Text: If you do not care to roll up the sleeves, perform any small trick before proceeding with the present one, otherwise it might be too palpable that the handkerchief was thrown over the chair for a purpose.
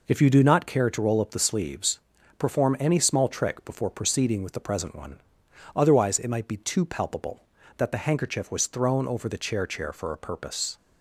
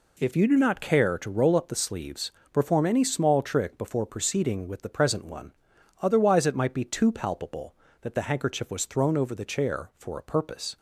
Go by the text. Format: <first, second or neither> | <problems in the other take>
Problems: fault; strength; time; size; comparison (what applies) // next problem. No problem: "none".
second | says "chair" twice; at 9.6 s